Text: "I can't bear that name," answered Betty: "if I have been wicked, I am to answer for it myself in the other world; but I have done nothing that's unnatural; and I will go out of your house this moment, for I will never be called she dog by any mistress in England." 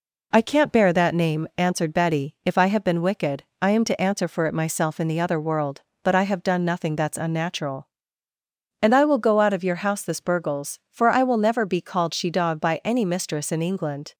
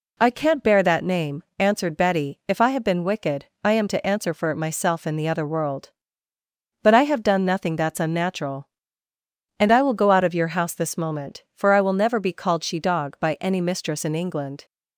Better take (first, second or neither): second